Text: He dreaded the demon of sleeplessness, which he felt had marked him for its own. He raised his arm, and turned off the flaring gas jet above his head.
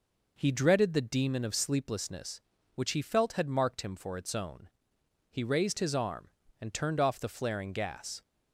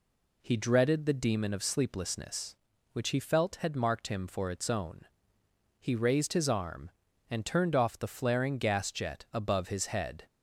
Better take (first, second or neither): second